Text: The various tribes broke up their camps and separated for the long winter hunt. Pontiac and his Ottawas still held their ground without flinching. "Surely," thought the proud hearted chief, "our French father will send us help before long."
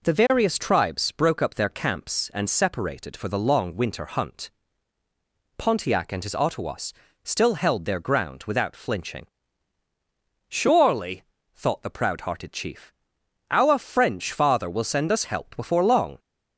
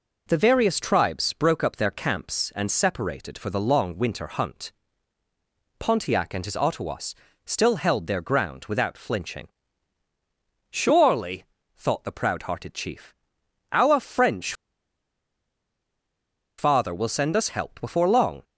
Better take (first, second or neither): first